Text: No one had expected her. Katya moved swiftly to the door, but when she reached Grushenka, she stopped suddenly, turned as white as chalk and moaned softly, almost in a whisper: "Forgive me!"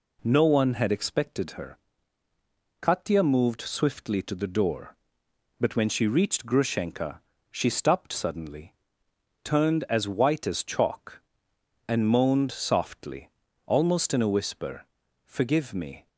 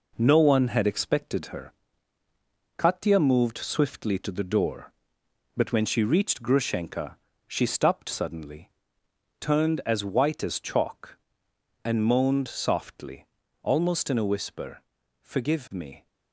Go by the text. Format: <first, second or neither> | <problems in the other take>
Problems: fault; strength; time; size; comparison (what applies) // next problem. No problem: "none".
first | gets quieter; noticeable; throughout; 6 dB